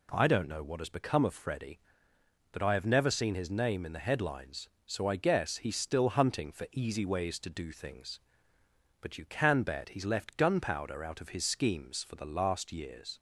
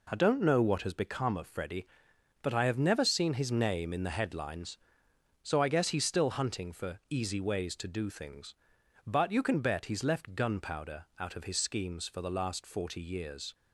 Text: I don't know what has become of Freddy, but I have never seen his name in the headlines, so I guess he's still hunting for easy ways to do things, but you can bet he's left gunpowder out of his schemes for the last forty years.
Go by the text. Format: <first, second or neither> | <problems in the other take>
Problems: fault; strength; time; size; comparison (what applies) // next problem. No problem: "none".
second | skips "forty"; at 12.7 s